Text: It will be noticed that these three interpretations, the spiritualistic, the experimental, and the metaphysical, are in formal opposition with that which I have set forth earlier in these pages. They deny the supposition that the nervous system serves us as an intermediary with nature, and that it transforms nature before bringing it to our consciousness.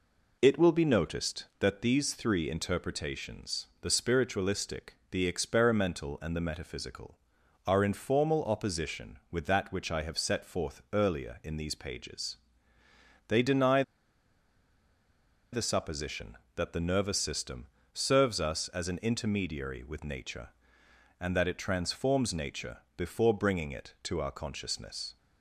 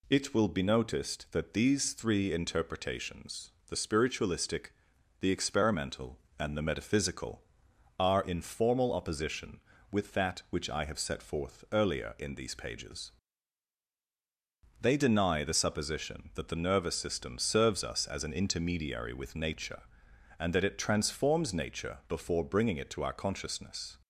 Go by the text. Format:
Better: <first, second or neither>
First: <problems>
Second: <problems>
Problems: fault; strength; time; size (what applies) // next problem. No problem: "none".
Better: second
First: pauses between "deny" and "the"; strong; at 13.8 s; 1.7 s long // pauses between "system" and "serves"; slight; at 17.6 s; 0.26 s long // pauses between "nature" and "before"; slight; at 22.7 s; 0.18 s long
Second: none